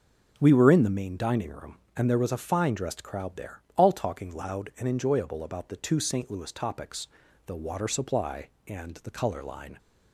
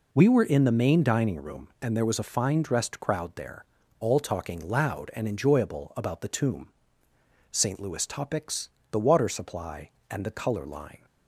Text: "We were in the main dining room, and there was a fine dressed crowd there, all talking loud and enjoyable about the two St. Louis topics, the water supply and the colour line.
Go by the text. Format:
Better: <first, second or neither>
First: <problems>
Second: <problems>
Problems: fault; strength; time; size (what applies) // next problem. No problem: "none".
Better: first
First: none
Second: says "tomb" for "two"; at 6.2 s